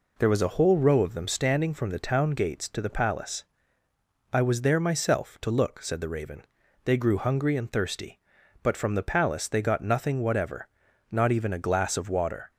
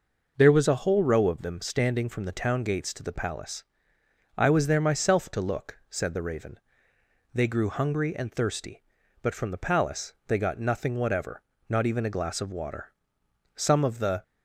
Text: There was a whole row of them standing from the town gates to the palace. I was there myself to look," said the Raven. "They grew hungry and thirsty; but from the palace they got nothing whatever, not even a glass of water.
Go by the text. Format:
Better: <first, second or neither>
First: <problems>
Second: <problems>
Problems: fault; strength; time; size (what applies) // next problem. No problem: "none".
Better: first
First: none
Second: pauses between "palace" and "they"; slight; at 10.1 s; 0.16 s long // goes on to say "Some of the"; noticeable; from 13.5 s on; 0.66 s long